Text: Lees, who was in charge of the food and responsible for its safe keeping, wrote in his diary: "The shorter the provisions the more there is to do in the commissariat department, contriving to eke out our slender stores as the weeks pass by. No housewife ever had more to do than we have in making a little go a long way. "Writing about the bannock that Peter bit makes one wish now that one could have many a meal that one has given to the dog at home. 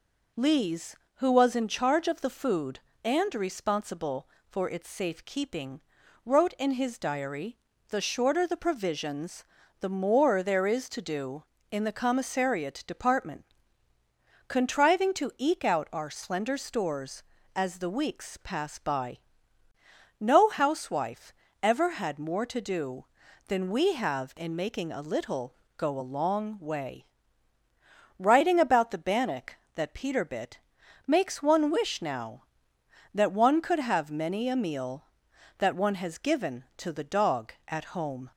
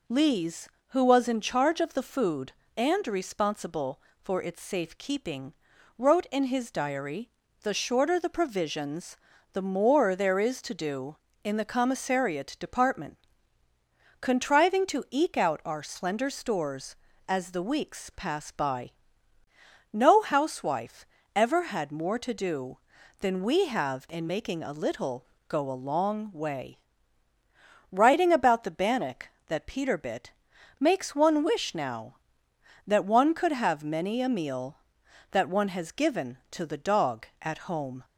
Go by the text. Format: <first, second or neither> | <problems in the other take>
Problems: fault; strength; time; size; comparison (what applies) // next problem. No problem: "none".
neither | pauses between "provisions" and "the"; slight; the same in both // pauses between "housewife" and "ever"; slight; the same in both // pauses between "little" and "go"; slight; the same in both // pauses between "bit" and "makes"; noticeable; the same in both